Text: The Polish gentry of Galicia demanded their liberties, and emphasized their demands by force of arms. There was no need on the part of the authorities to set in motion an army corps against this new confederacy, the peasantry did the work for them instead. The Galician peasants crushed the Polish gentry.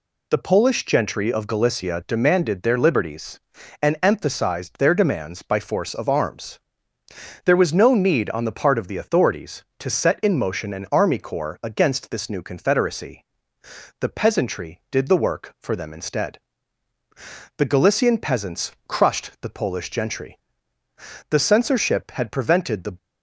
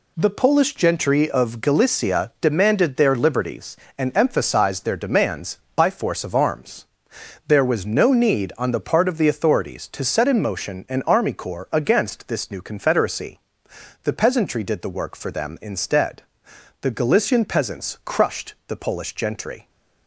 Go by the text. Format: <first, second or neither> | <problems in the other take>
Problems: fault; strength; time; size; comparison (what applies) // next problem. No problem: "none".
second | pauses between "peasants" and "crushed"; slight; at 18.7 s; 0.16 s long // goes on to say "The censorship had prevented the"; from 21.2 s on; 1.6 s long